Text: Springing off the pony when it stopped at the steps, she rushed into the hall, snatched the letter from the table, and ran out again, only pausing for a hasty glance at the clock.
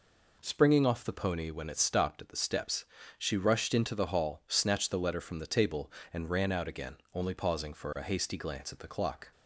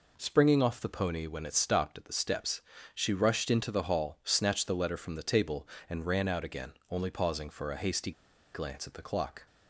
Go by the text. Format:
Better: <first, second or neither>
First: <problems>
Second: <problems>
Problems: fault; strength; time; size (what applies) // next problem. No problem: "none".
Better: first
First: none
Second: pauses between "hasty" and "glance"; at 8.1 s; 0.43 s long